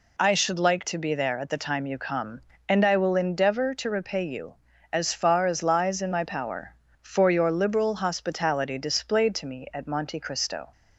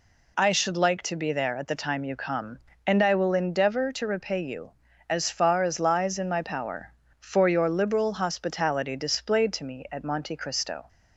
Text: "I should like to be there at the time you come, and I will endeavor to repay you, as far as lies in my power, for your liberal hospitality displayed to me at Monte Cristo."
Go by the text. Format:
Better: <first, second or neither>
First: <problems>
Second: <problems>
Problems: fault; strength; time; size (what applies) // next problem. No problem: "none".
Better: neither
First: none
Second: none